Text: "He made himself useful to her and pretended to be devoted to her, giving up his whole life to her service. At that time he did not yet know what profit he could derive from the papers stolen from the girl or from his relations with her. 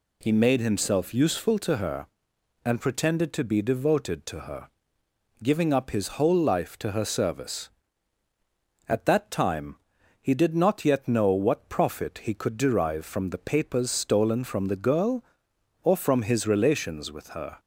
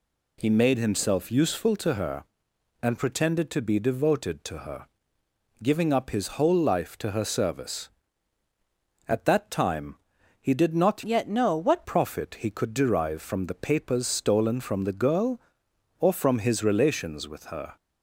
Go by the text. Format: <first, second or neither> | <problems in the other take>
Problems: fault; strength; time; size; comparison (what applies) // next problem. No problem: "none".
first | pauses between "time" and "he"; at 9.9 s; 0.42 s long; also in the first // changes voice from "yet" to "what"; from 11.0 to 11.8 s; 0.8 s long